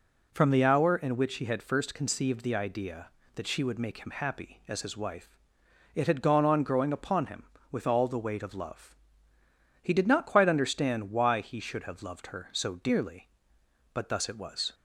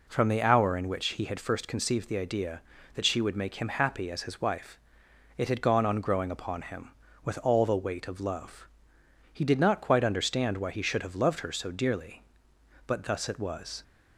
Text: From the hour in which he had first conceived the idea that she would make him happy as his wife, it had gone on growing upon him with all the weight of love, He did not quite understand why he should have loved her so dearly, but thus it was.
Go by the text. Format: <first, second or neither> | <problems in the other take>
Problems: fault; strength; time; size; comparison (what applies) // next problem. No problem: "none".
neither | none